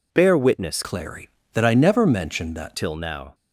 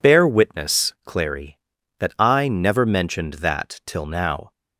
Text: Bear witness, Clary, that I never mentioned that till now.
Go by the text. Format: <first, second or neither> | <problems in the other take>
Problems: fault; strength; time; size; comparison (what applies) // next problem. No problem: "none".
second | changes voice from "Clary" to "that"; from 0.8 to 2.7 s; 1.9 s long